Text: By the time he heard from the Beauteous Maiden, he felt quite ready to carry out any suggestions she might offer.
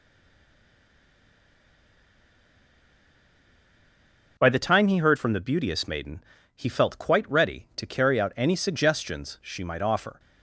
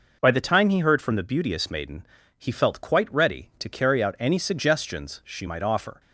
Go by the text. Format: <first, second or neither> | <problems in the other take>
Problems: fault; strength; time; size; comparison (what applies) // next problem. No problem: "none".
second | stays silent before the first word; strong; until 4.3 s; 4.3 s long